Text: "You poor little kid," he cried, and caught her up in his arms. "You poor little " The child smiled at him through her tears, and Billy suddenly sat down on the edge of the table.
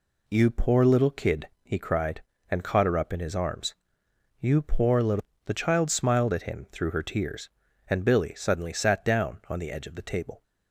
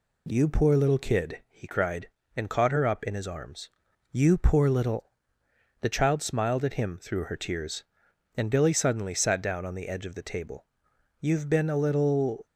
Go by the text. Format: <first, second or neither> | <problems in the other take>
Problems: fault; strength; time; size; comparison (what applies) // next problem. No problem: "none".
first | goes on to say "You've been a little"; noticeable; from 11.1 s on; 1.2 s long